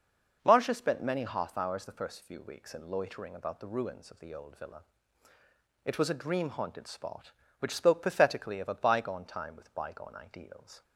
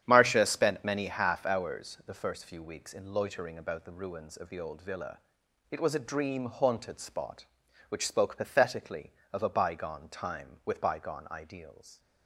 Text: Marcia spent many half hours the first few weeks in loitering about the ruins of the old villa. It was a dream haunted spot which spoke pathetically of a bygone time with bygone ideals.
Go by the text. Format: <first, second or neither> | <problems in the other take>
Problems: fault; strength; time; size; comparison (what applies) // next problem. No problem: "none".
first | starts louder than the rest; strong; until 1.8 s; 9.5 dB